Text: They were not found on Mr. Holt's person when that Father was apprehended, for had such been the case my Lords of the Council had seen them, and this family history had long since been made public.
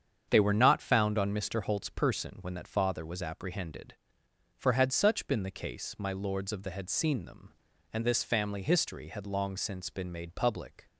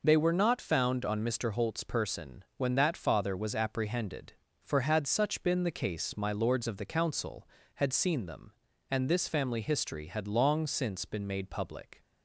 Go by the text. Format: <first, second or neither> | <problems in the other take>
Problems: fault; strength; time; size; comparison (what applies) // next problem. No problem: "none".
second | starts louder than the rest; strong; until 1.2 s; 7.5 dB // skips "Council"; at 6.7 s